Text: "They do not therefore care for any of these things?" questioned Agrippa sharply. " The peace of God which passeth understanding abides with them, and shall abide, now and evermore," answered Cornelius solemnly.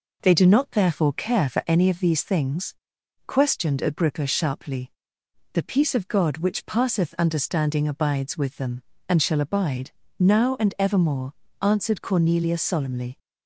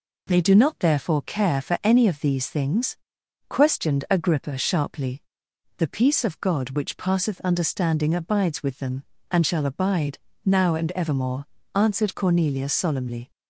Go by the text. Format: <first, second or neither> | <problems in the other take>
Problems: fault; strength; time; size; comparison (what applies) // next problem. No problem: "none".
neither | none